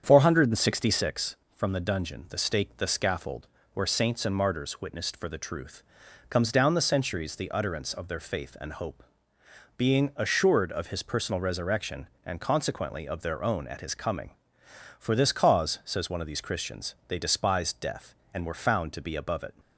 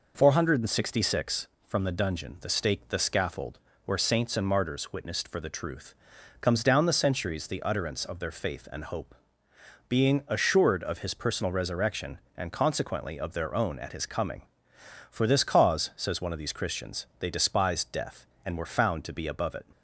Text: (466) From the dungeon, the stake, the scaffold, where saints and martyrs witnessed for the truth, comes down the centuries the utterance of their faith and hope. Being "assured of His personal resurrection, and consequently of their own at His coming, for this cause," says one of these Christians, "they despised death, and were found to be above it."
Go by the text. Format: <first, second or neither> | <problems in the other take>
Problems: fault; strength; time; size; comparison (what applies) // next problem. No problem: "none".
second | starts louder than the rest; strong; until 1.0 s; 8 dB